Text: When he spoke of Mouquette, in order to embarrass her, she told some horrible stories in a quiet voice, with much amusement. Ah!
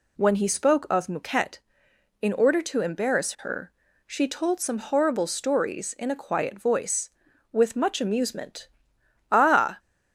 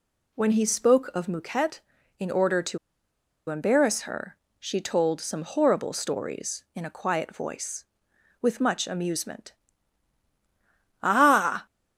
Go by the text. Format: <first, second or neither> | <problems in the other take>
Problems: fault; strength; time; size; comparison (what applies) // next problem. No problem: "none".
first | pauses between "to" and "embarrass"; noticeable; at 2.7 s; 0.71 s long